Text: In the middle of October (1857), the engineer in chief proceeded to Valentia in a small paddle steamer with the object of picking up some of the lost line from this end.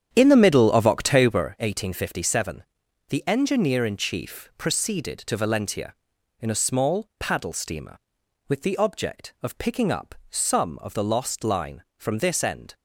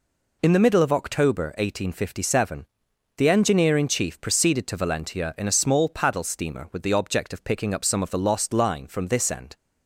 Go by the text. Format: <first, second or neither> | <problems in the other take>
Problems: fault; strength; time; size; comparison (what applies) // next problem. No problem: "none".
second | starts louder than the rest; strong; until 1.5 s; 8.5 dB // pauses between "up" and "some"; slight; at 10.1 s; 0.16 s long